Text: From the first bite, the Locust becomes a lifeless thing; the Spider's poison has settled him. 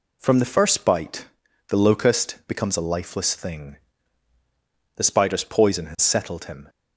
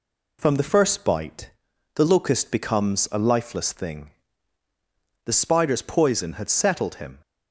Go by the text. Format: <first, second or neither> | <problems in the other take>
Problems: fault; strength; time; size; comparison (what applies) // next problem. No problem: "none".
first | says "had" for "has"; at 6.3 s